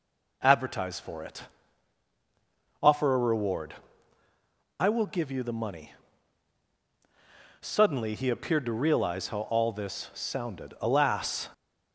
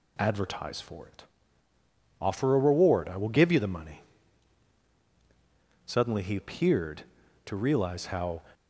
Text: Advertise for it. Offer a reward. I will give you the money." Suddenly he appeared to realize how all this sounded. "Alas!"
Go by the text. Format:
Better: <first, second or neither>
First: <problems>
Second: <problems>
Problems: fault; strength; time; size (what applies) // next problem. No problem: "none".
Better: first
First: none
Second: stops before "all this sounded Alas"; at 8.5 s